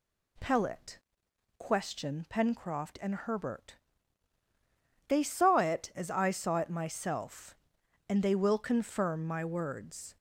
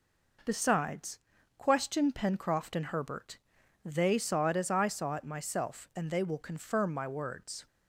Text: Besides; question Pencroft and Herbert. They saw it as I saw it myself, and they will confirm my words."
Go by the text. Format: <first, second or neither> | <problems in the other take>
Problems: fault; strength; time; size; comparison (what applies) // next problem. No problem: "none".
second | says "Pellet" for "Besides"; at 0.3 s